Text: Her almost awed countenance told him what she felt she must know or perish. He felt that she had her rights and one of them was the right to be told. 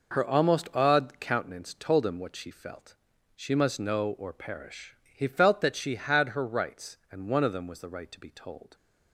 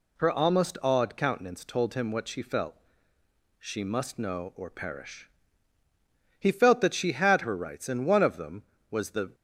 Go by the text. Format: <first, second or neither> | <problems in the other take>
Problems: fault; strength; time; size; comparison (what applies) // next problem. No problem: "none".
first | pauses between "felt" and "she"; noticeable; at 2.7 s; 0.82 s long; also in the first // stops before "right to be told"; at 9.3 s